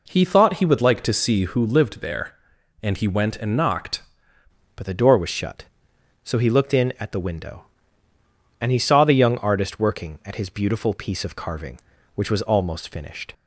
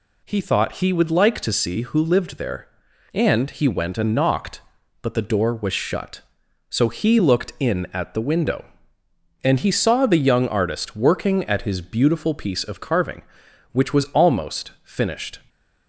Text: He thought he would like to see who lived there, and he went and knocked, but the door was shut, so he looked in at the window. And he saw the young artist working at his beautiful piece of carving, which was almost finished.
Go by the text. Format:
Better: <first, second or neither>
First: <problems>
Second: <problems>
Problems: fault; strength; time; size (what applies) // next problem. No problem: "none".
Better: second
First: changes voice at "but"; from 4.7 s on; 8.6 s long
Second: none